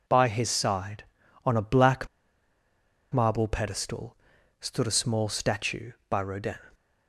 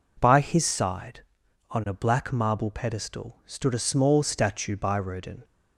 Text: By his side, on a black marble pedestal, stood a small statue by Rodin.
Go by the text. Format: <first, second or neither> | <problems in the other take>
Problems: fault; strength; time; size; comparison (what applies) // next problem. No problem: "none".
second | pauses between "black" and "marble"; at 2.0 s; 1.0 s long